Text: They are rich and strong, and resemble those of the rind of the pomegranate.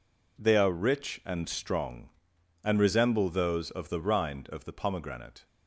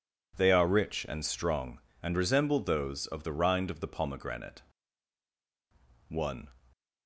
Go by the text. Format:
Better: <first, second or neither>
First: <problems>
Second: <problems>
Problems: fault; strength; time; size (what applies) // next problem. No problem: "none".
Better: first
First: none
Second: goes on to say "One"; slight; from 6.0 s on; 0.40 s long